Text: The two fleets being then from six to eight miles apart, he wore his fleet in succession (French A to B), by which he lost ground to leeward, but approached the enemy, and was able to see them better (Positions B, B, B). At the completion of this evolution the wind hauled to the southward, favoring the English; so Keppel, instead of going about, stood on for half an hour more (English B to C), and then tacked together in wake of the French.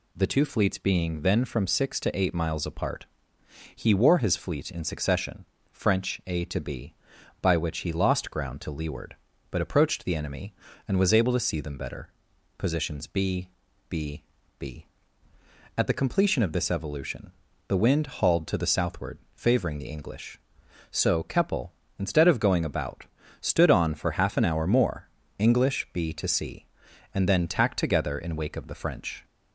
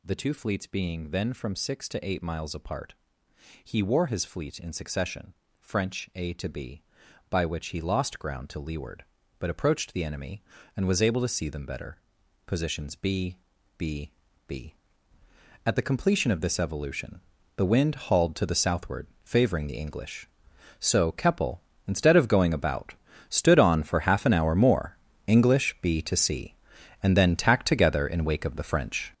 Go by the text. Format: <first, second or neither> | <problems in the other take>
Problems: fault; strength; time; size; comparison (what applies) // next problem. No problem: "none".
first | gets louder; strong; throughout; 9.5 dB // pauses between "evolution" and "the"; at 17.1 s; 0.38 s long; also in the first